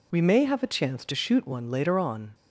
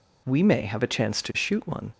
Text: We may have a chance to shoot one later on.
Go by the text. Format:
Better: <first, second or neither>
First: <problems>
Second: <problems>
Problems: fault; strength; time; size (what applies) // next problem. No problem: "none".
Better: first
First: none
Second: stops before "later on"; at 1.9 s